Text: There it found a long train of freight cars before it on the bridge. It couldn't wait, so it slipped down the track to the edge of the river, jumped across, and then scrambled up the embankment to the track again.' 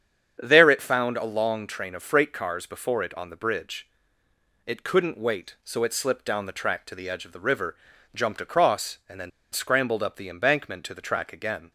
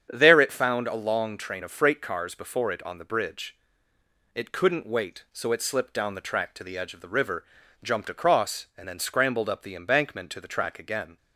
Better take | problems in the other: second | starts louder than the rest; strong; until 1.4 s; 8 dB; strong in the second // pauses between "then" and "scrambled"; slight; at 9.3 s; 0.23 s long

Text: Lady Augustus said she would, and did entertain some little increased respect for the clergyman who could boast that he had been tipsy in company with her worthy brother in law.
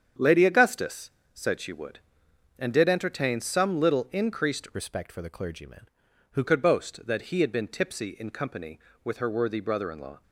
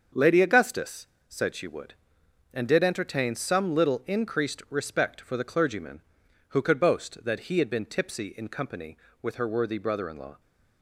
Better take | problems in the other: second | starts louder than the rest; strong; until 1.4 s; 8 dB; also in the second // pauses between "Augustus" and "said"; slight; at 1.1 s; 0.24 s long; slight in the second // changes voice from "respect" to "who"; from 4.7 to 6.4 s; 1.7 s long

